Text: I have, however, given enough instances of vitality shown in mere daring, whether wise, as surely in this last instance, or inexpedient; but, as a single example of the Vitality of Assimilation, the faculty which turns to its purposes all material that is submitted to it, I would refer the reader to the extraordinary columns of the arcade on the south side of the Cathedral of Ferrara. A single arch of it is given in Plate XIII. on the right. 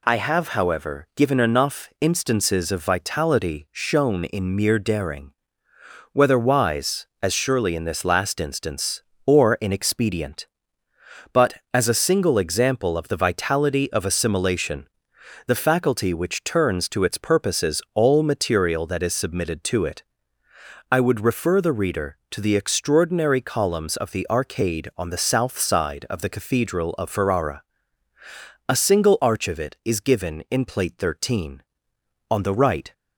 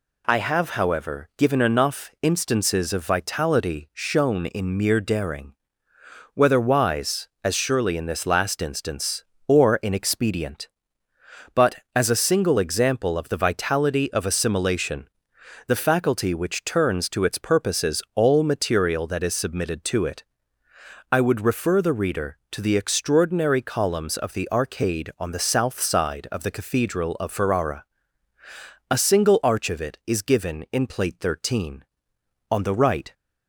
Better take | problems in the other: neither | none

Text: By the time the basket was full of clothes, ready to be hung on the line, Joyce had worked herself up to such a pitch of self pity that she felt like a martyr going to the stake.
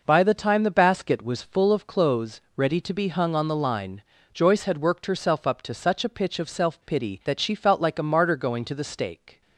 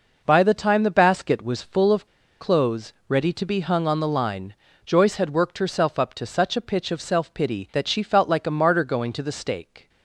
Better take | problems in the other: first | pauses between "of" and "clothes"; slight; at 2.0 s; 0.34 s long

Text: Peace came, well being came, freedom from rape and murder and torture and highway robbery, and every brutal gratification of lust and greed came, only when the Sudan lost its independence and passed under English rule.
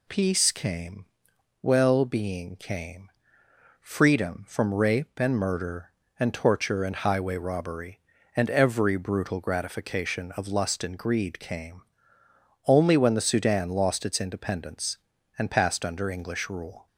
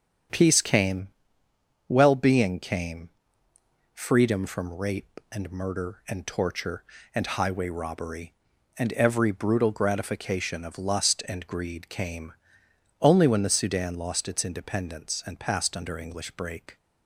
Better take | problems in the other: first | starts louder than the rest; strong; until 2.1 s; 8 dB // says "break" for "rule"; at 16.3 s

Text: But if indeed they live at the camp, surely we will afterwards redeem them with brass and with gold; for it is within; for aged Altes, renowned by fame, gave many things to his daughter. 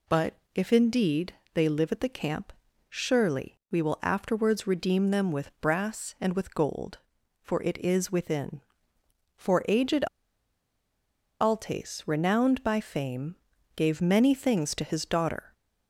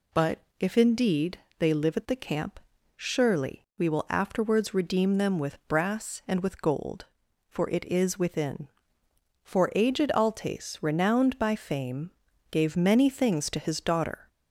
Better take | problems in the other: second | pauses between "But" and "if"; slight; at 0.3 s; 0.18 s long; slight in the second // pauses between "indeed" and "they"; slight; at 1.3 s; 0.18 s long; slight in the second // pauses between "aged" and "Altes"; strong; at 10.0 s; 1.3 s long

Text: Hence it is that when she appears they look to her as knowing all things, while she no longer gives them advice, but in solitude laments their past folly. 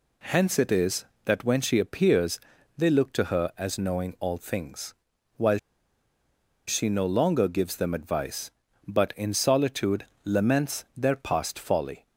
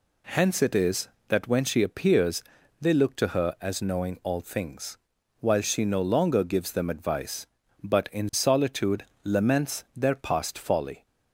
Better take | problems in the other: second | pauses between "appears" and "they"; at 2.3 s; 0.38 s long; also in the second // pauses between "while" and "she"; at 5.5 s; 1.0 s long // pauses between "solitude" and "laments"; slight; at 10.0 s; 0.20 s long; slight in the second

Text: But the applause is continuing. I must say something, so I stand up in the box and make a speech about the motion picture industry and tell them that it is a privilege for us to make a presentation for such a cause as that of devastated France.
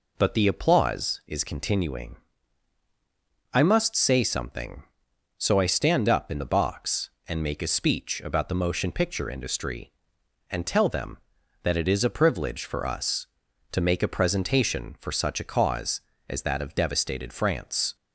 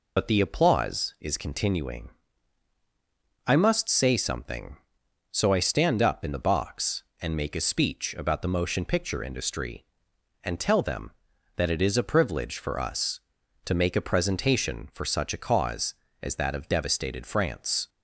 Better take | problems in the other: first | loses the start of "But"; at 0.1 s; 60 ms

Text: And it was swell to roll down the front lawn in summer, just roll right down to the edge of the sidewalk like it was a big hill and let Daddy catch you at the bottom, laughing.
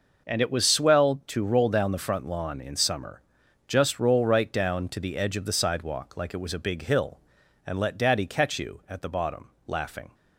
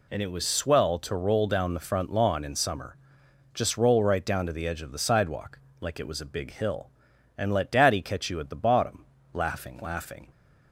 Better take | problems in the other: first | pauses between "sidewalk" and "like"; slight; at 5.5 s; 0.22 s long // says "laughing" twice; at 9.8 s

